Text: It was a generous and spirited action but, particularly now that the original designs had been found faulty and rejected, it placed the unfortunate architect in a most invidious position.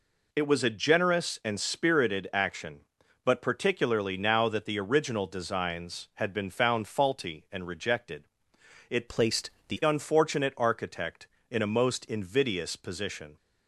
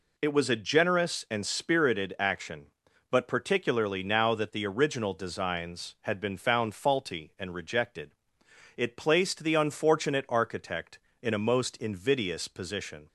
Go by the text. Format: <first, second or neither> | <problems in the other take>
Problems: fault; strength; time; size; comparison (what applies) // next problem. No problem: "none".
second | changes voice from "placed" to "the"; from 9.0 to 9.8 s; 0.8 s long // pauses between "placed" and "the"; slight; at 9.4 s; 0.20 s long